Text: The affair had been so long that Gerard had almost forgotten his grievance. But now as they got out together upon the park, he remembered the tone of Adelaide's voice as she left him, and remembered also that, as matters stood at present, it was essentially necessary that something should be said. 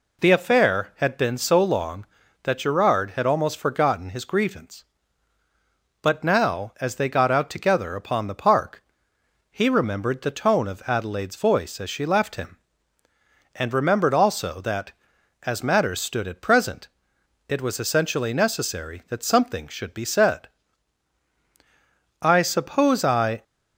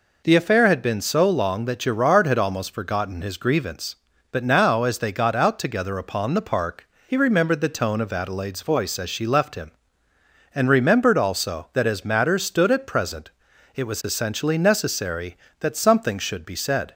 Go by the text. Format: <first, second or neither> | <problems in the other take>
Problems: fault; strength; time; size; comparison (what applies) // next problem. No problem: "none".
second | goes on to say "I suppose I"; noticeable; from 22.2 s on; 1.2 s long